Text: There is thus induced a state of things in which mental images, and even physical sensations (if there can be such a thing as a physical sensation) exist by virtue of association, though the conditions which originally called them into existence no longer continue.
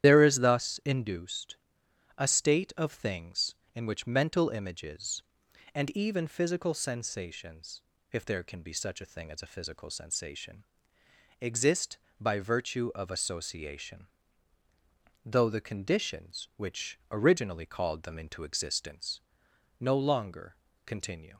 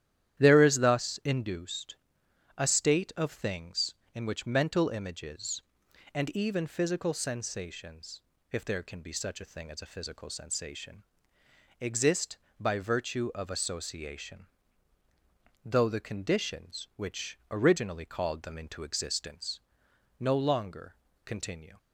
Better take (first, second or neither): second